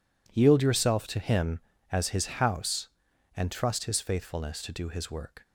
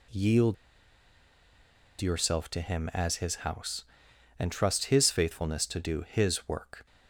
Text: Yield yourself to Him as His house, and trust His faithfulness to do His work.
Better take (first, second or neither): first